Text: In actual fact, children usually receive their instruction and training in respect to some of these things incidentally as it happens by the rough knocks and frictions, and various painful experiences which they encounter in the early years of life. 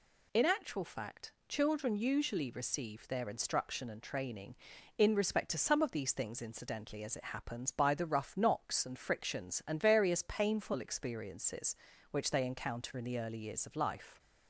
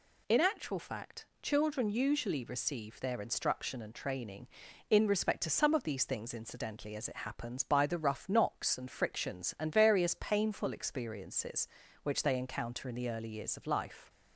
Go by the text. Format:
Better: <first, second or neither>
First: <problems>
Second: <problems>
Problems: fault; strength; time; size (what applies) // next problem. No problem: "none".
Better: neither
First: none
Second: none